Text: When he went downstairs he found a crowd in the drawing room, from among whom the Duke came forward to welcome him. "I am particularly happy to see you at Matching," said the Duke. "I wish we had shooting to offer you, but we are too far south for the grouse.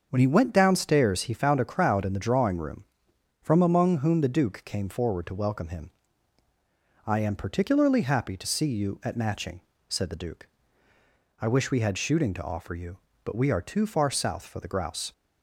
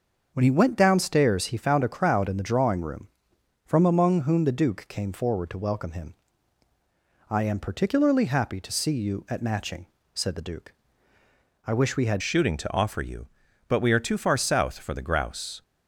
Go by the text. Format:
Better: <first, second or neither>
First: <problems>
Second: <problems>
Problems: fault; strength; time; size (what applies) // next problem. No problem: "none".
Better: first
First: starts louder than the rest; until 1.1 s; 6.5 dB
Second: starts louder than the rest; until 1.3 s; 6.5 dB // changes voice at "shooting"; from 12.1 s on; 3.5 s long